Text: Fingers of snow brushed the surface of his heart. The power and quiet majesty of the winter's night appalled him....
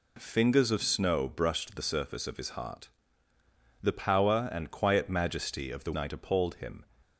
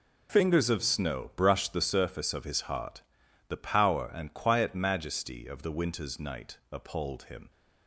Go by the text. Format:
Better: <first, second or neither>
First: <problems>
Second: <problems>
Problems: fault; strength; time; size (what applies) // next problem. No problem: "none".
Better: second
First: skips "winter's"; at 5.9 s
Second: none